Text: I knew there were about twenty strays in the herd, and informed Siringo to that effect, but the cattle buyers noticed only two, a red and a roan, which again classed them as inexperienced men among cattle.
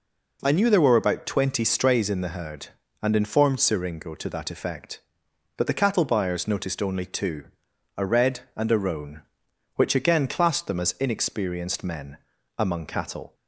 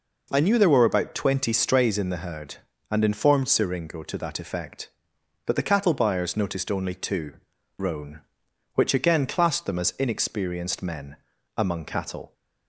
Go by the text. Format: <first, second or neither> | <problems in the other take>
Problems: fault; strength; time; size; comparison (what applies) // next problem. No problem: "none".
first | skips "a red and a"; at 7.5 s // pauses between "men" and "among"; at 11.1 s; 0.42 s long; also in the first